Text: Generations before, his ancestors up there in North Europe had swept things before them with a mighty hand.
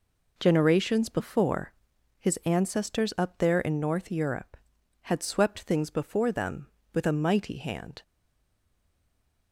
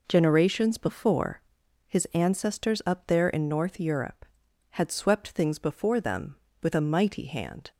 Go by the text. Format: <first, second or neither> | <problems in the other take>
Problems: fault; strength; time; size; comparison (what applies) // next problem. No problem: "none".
second | stays silent after the last word; noticeable; from 8.0 s on; 1.5 s long